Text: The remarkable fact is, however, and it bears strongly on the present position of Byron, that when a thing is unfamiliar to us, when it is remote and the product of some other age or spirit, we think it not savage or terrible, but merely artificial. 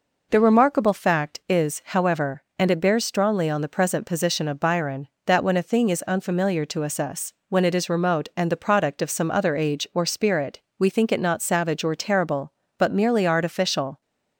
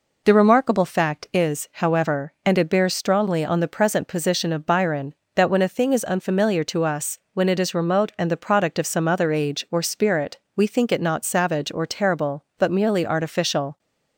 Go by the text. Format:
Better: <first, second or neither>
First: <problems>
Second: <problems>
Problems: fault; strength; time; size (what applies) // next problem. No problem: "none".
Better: second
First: says "us" twice; at 6.9 s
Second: none